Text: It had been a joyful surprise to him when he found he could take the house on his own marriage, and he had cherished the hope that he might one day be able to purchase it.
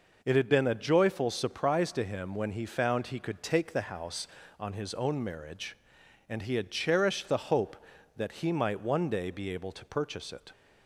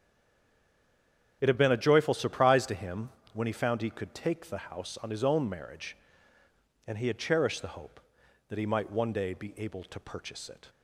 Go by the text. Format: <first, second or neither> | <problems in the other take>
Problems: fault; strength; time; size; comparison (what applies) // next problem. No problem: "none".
first | stays silent before the first word; noticeable; until 1.4 s; 1.4 s long // starts louder than the rest; strong; until 2.4 s; 8.5 dB // pauses between "him" and "when"; slight; at 3.0 s; 0.22 s long